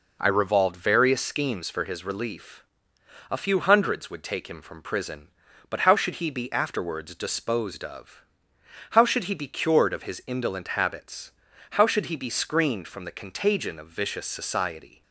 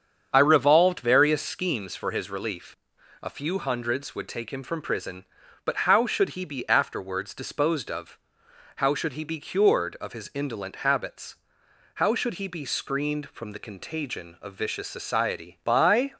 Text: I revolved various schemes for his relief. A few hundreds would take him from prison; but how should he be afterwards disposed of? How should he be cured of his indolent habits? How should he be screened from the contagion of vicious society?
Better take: first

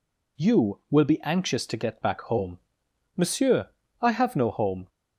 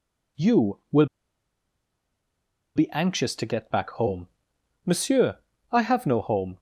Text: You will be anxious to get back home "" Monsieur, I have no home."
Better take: first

